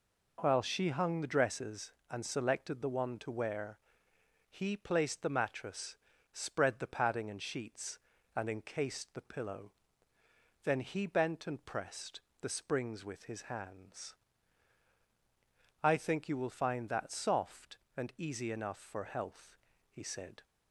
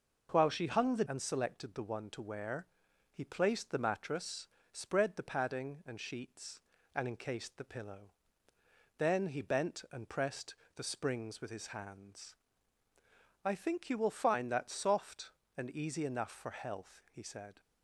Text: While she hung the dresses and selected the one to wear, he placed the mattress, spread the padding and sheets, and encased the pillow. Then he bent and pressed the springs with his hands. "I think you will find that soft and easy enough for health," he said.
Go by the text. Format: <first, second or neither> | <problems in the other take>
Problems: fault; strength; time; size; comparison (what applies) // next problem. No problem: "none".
first | skips "dresses"; at 1.0 s // pauses between "pressed" and "the"; slight; at 10.5 s; 0.20 s long; slight in the first